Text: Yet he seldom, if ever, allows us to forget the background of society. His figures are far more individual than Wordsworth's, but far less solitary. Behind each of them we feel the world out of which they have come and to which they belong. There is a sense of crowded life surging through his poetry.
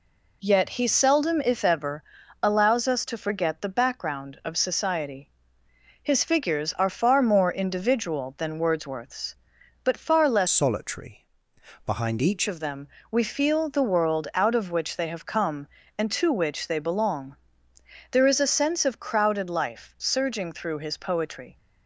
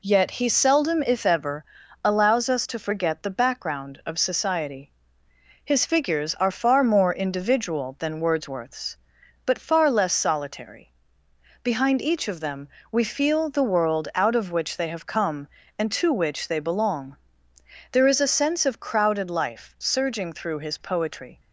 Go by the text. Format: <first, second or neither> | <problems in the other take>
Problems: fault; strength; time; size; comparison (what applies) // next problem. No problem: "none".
second | changes voice from "solitary" to "each"; from 10.4 to 12.4 s; 2.0 s long // pauses between "them" and "we"; slight; at 12.8 s; 0.22 s long; slight in the second